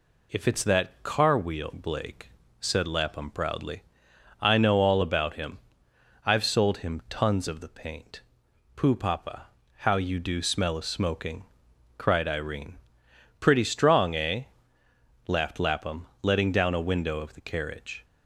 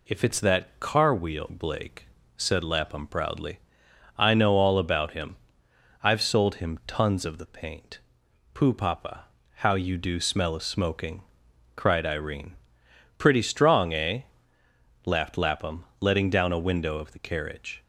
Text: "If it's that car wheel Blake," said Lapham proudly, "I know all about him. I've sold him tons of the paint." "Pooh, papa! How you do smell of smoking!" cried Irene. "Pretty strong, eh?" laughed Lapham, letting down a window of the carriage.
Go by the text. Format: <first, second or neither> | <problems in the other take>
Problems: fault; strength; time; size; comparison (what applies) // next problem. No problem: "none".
neither | none